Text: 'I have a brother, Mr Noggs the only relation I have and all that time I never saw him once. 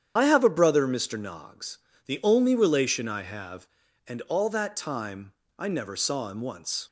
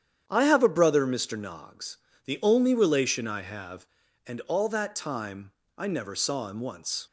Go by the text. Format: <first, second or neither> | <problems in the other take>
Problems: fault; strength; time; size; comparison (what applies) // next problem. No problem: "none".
second | loses the start of "I"; at 0.1 s; 65 ms // starts louder than the rest; strong; until 1.1 s; 9 dB; strong in the second // pauses between "Noggs" and "the"; slight; at 1.7 s; 0.26 s long; slight in the second // pauses between "time" and "I"; slight; at 5.3 s; 0.26 s long; slight in the second